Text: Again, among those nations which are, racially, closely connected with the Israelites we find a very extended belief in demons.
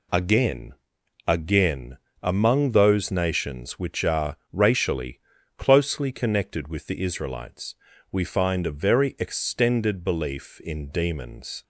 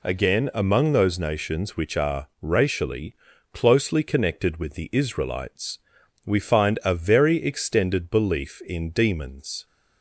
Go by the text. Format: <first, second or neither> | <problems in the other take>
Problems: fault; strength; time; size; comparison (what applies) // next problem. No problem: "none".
second | says "Again" twice; at 1.2 s // pauses between "Israelites" and "we"; slight; at 7.7 s; 0.36 s long; noticeable in the second